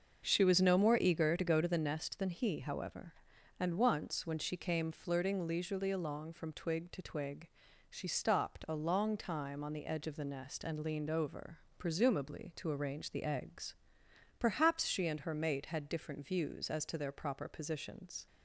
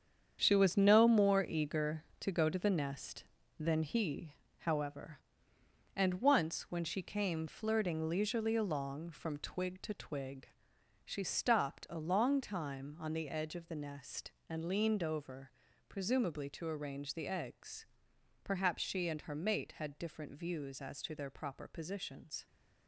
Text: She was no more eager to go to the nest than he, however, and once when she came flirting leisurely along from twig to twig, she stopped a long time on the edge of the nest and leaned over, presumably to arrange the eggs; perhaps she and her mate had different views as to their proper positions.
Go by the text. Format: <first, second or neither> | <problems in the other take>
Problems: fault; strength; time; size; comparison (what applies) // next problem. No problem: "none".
first | gets quieter; strong; throughout; 9.5 dB // starts louder than the rest; strong; until 1.4 s; 8 dB; also in the first